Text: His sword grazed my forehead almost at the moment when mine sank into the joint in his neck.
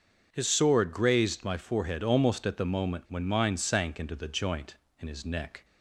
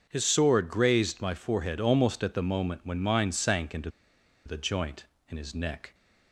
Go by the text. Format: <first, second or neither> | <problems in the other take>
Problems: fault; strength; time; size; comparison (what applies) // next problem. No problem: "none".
first | starts louder than the rest; until 1.1 s; 6.5 dB; also in the first // pauses between "into" and "the"; noticeable; at 3.8 s; 0.56 s long